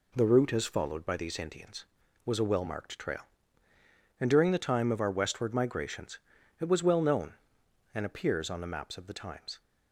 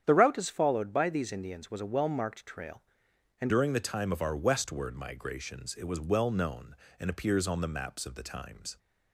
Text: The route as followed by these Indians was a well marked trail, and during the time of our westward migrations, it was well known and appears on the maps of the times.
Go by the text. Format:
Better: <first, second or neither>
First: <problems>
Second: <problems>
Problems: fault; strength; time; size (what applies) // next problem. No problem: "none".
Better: first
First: none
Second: starts louder than the rest; strong; until 1.0 s; 9 dB // changes voice at "during"; from 3.4 s on; 5.3 s long